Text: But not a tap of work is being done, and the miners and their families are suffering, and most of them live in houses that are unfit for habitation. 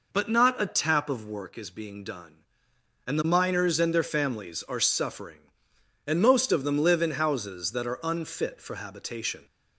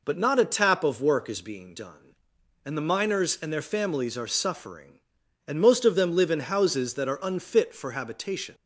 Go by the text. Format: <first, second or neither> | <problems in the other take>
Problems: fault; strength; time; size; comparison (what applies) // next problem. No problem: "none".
neither | none